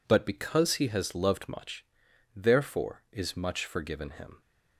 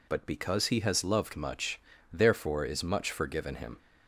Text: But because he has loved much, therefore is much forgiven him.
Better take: neither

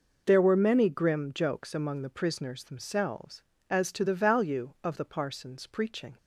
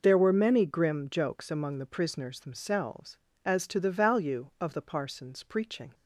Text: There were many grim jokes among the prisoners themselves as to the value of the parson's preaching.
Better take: neither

